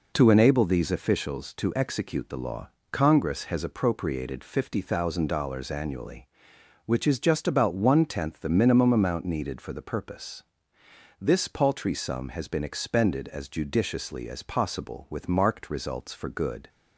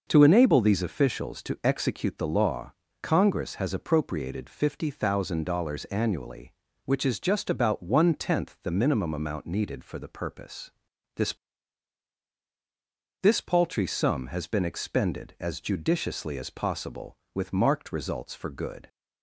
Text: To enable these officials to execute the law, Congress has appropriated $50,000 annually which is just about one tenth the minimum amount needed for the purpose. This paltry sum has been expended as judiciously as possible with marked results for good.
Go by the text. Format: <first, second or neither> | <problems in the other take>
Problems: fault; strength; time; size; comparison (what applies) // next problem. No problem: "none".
first | says "This" twice; at 13.2 s